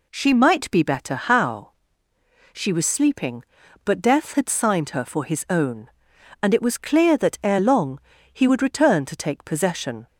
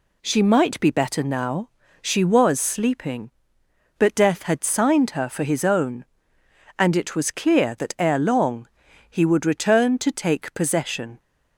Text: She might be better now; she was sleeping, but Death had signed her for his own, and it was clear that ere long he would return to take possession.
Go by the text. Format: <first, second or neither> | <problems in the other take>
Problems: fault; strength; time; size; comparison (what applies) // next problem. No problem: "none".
second | says "how" for "now"; at 1.1 s // pauses between "long" and "he"; slight; at 8.0 s; 0.32 s long; also in the second